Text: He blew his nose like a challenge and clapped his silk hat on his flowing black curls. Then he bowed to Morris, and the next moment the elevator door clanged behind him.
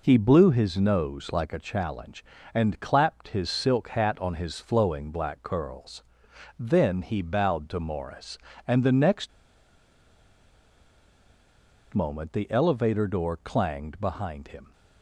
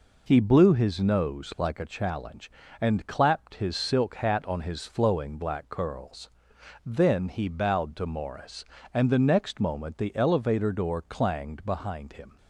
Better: second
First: pauses between "next" and "moment"; strong; at 9.2 s; 2.6 s long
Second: none

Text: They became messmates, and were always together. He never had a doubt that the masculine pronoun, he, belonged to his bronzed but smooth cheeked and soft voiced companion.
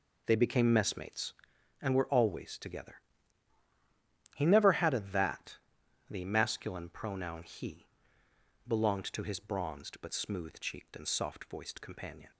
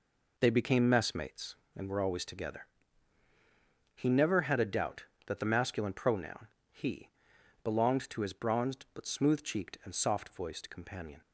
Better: second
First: skips "doubt"; at 5.0 s // pauses between "that" and "the"; noticeable; at 5.5 s; 0.50 s long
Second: none

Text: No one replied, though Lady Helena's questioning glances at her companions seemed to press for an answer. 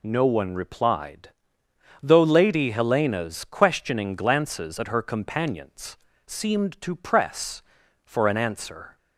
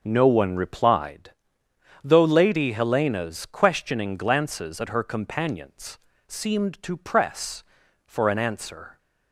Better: first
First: pauses between "companions" and "seemed"; slight; at 5.9 s; 0.28 s long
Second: starts louder than the rest; until 1.1 s; 6 dB // pauses between "companions" and "seemed"; slight; at 5.9 s; 0.28 s long

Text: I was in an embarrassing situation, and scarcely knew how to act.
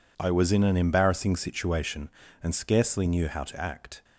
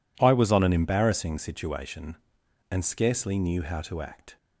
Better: first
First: none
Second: says "on" for "in"; at 0.4 s

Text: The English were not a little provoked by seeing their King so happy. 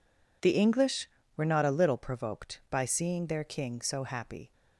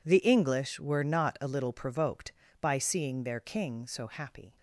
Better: neither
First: none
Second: none

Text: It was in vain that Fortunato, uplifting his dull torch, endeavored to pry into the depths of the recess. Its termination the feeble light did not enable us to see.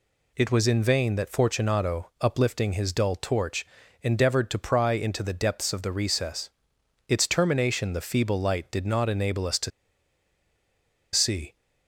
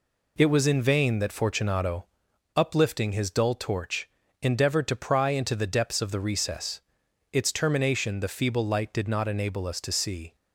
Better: second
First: pauses between "to" and "see"; strong; at 9.7 s; 1.4 s long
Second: none

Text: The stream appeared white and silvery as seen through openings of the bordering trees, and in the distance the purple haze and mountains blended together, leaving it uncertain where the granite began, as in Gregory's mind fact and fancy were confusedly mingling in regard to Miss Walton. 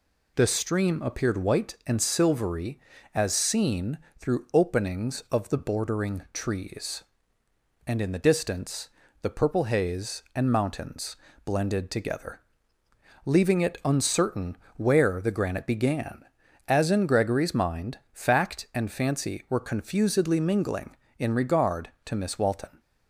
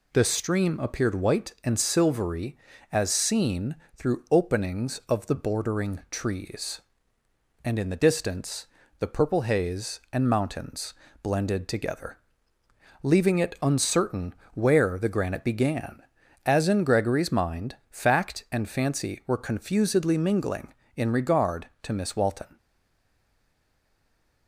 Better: first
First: pauses between "seen" and "through"; slight; at 3.9 s; 0.18 s long // pauses between "distance" and "the"; slight; at 8.8 s; 0.32 s long // pauses between "mountains" and "blended"; slight; at 11.1 s; 0.30 s long // pauses between "uncertain" and "where"; slight; at 14.5 s; 0.18 s long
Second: pauses between "seen" and "through"; slight; at 3.7 s; 0.18 s long // pauses between "distance" and "the"; slight; at 8.6 s; 0.32 s long // pauses between "mountains" and "blended"; slight; at 10.9 s; 0.30 s long // pauses between "uncertain" and "where"; slight; at 14.3 s; 0.18 s long // stays silent after the last word; noticeable; from 22.5 s on; 1.9 s long

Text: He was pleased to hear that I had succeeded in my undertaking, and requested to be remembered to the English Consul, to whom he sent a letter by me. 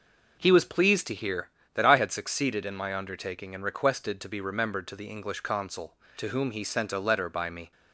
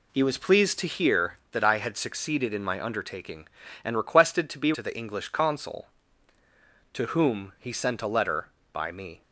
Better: first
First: none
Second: skips "remembered"; at 4.7 s

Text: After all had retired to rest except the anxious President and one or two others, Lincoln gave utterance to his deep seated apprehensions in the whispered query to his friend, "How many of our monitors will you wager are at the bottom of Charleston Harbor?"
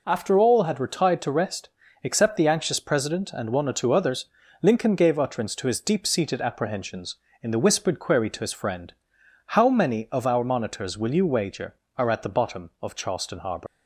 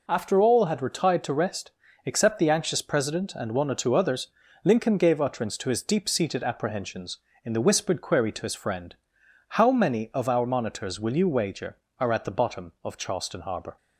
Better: second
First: pauses between "rest" and "except"; slight; at 1.6 s; 0.34 s long // leaves "Harbor" unfinished; at 13.6 s; 80 ms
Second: pauses between "rest" and "except"; slight; at 1.7 s; 0.34 s long

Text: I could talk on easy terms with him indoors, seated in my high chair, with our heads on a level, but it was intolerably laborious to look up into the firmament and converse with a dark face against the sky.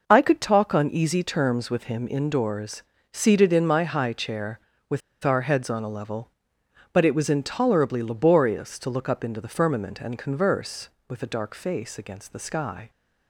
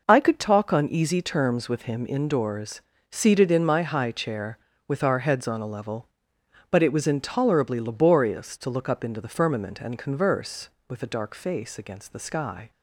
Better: second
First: pauses between "with" and "our"; slight; at 5.0 s; 0.23 s long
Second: none

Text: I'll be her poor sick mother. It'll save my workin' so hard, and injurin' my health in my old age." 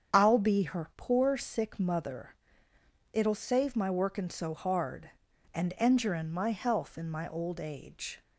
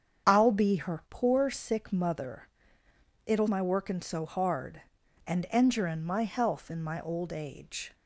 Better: first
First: starts louder than the rest; strong; until 1.2 s; 8 dB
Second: starts louder than the rest; strong; until 1.3 s; 8 dB // skips "save"; at 3.4 s

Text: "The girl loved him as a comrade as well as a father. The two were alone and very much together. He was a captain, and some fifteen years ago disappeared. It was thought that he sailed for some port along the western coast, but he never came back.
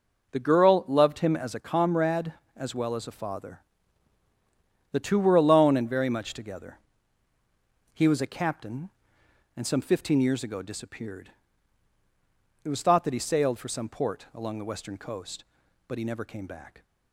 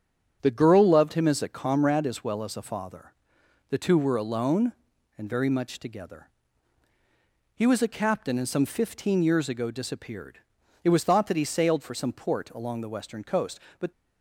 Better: first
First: none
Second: starts louder than the rest; strong; until 1.4 s; 7.5 dB // stops before "he never came back"; at 13.9 s

